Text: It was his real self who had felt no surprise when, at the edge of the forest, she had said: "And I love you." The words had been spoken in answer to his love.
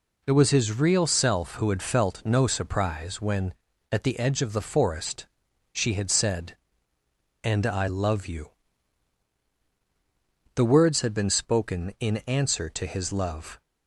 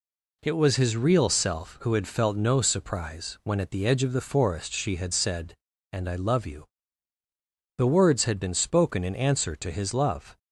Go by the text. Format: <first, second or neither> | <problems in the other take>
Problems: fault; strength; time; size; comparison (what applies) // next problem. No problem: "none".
neither | none